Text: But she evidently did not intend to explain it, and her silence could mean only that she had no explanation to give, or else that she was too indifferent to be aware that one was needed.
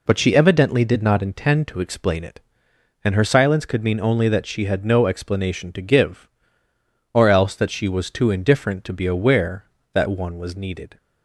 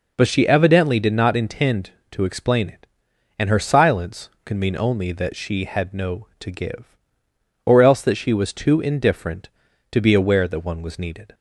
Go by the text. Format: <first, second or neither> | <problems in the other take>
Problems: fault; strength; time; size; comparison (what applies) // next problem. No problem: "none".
first | skips "explanation"; at 6.3 s